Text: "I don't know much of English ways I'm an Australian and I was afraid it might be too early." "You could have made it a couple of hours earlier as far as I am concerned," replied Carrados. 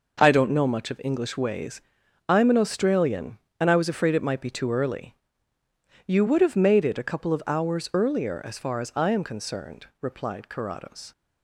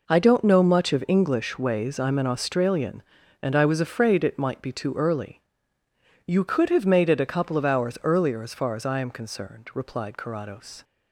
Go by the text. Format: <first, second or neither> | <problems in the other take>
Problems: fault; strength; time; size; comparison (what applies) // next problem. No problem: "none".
second | pauses between "ways" and "I'm"; noticeable; at 1.8 s; 0.48 s long // says "would" for "could"; at 6.2 s